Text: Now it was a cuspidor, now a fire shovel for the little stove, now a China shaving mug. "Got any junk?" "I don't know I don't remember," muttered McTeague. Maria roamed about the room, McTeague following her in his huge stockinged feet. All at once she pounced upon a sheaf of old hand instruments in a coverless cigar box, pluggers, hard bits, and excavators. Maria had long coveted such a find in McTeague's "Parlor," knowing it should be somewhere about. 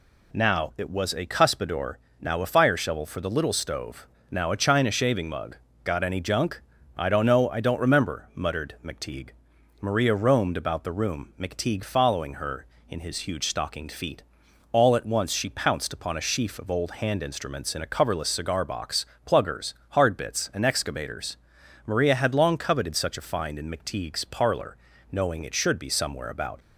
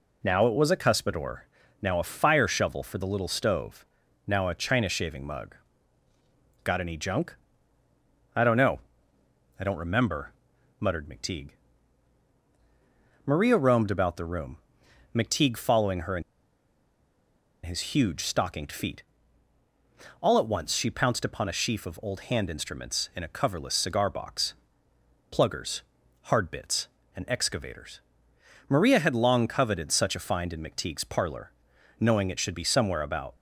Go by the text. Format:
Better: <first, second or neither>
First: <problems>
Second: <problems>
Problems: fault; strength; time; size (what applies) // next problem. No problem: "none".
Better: first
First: none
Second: pauses between "know" and "I"; noticeable; at 8.7 s; 0.80 s long // pauses between "in" and "his"; strong; at 16.2 s; 1.4 s long